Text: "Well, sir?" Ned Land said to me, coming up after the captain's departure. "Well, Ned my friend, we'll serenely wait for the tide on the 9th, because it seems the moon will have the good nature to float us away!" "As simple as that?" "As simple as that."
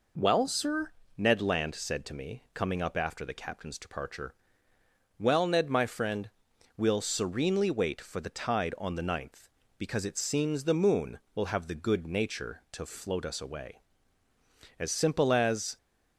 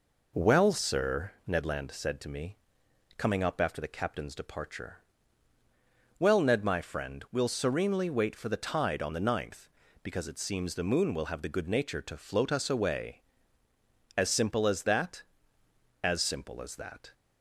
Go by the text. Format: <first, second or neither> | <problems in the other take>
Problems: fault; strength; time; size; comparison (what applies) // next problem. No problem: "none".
second | stops before "that As simple as that"; at 15.7 s